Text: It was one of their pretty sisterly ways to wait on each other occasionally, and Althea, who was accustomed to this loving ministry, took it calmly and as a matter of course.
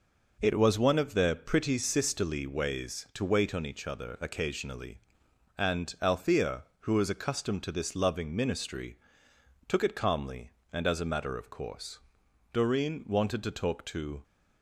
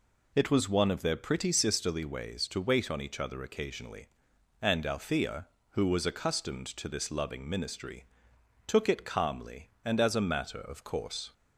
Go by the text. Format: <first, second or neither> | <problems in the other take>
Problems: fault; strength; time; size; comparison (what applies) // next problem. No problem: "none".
second | goes on to say "Doreen wanted to talk to"; strong; from 12.5 s on; 1.7 s long